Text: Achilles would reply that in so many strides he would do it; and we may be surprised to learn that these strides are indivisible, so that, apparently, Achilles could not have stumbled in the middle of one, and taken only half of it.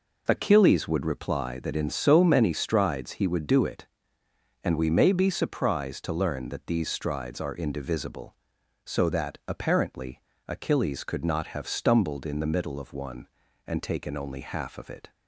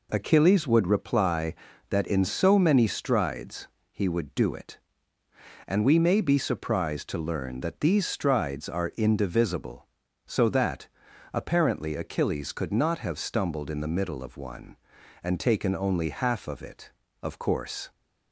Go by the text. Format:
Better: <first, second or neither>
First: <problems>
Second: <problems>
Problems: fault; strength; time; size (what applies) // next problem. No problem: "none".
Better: first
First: none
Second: pauses between "strides" and "he"; slight; at 3.6 s; 0.24 s long // goes on to say "Of course"; noticeable; from 17.2 s on; 0.68 s long